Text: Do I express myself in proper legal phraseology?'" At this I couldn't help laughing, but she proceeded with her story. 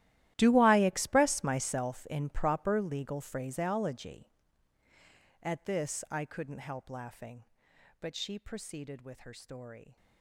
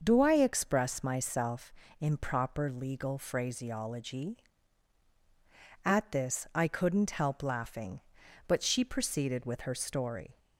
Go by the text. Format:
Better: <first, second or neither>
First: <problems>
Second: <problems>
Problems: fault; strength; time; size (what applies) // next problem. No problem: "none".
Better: second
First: gets quieter; strong; throughout; 18 dB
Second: none